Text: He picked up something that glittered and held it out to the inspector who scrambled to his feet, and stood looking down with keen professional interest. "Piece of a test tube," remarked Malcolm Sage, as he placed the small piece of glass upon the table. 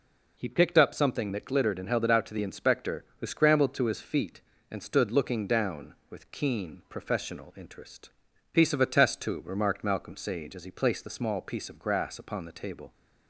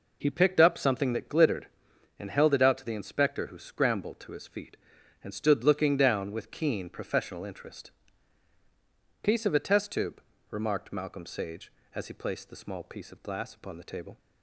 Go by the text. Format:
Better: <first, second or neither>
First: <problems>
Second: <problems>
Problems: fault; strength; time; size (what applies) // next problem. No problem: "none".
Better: second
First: says "grass" for "glass"; at 11.7 s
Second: none